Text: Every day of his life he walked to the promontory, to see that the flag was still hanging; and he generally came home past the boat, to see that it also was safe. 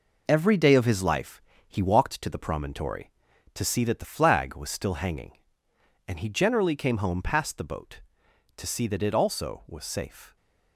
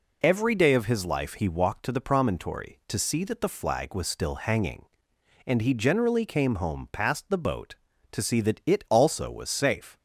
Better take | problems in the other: second | gets quieter; throughout; 7 dB // pauses between "life" and "he"; slight; at 1.3 s; 0.28 s long

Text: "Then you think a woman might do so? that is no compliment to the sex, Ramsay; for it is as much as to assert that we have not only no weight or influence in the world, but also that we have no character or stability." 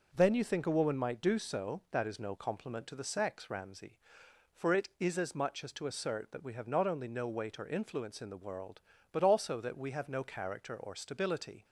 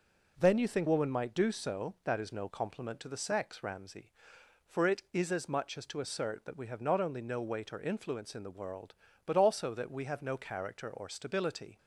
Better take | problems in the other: first | skips "a"; at 0.8 s

